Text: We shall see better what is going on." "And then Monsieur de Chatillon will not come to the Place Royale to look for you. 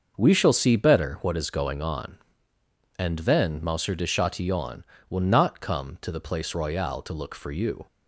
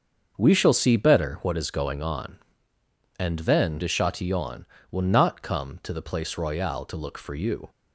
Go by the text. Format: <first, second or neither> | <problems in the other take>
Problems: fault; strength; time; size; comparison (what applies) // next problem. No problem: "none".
first | starts louder than the rest; until 1.3 s; 6.5 dB; also in the first // skips "Monsieur"; at 3.7 s